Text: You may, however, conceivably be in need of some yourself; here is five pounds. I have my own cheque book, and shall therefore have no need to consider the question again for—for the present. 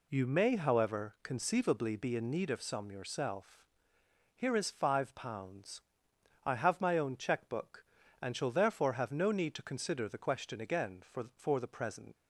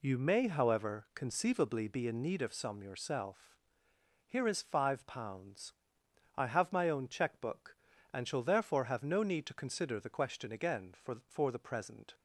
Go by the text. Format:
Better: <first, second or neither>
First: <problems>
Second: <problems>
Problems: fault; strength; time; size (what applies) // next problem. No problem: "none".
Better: second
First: leaves "present" unfinished; at 12.1 s; 60 ms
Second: none